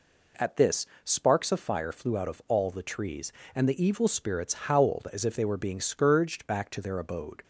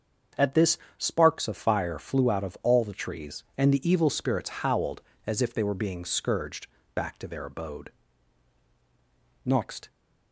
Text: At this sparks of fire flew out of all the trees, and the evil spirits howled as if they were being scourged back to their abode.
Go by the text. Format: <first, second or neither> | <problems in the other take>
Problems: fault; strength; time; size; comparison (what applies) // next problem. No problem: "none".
first | starts louder than the rest; until 1.5 s; 7 dB // pauses between "this" and "sparks"; slight; at 0.7 s; 0.20 s long; slight in the first // pauses between "scourged" and "back"; slight; at 6.6 s; 0.26 s long // goes on to say "Next"; slight; from 9.4 s on; 0.46 s long